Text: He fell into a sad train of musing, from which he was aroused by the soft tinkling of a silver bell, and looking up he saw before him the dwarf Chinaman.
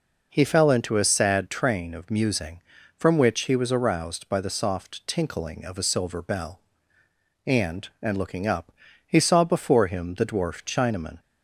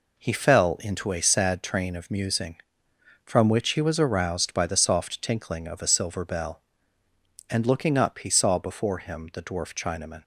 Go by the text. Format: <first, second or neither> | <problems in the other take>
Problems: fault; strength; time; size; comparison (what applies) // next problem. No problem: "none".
second | says "and" twice; at 8.0 s // pauses between "up" and "he"; slight; at 8.7 s; 0.34 s long